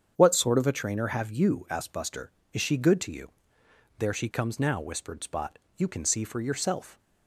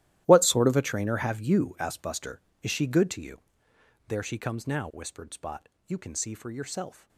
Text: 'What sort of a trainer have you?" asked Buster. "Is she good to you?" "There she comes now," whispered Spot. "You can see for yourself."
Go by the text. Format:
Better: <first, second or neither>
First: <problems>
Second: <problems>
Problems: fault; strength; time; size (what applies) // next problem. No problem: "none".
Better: first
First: starts louder than the rest; strong; until 1.1 s; 7.5 dB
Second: gets quieter; strong; throughout; 16 dB // starts louder than the rest; strong; until 1.2 s; 14 dB